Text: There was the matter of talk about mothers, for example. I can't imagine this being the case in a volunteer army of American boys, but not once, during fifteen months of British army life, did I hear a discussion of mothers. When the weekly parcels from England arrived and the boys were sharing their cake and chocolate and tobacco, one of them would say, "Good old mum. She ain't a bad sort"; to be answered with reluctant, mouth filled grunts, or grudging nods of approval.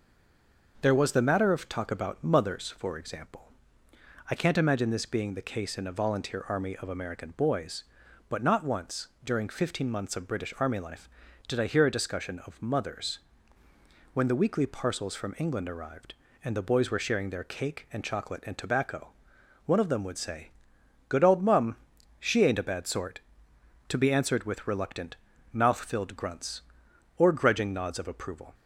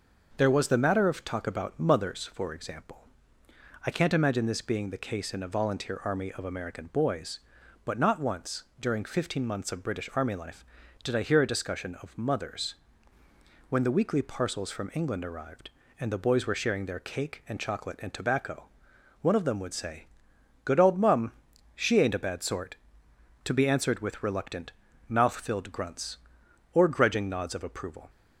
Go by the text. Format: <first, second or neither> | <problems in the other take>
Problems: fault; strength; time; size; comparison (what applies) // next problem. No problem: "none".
second | stays silent before the first word; slight; until 0.7 s; 0.7 s long // starts louder than the rest; noticeable; until 1.8 s; 6 dB; noticeable in the second